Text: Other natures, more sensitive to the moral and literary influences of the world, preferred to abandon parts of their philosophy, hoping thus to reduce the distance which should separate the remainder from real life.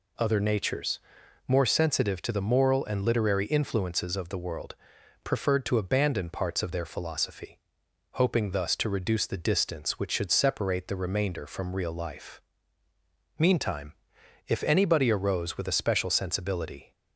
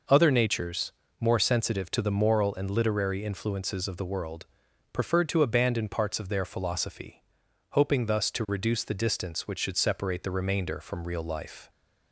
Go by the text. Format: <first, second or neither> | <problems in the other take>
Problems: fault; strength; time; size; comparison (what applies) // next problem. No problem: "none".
second | goes on to say "Meantime if anybody arose with a special sensibility"; strong; from 13.3 s on; 3.5 s long